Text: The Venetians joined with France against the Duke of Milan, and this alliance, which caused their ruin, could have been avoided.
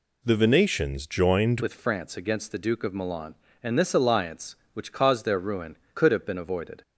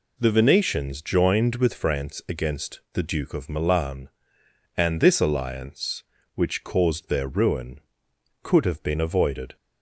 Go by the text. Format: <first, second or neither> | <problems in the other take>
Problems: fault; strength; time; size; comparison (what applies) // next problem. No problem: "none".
second | changes voice at "with"; from 1.6 s on; 5.2 s long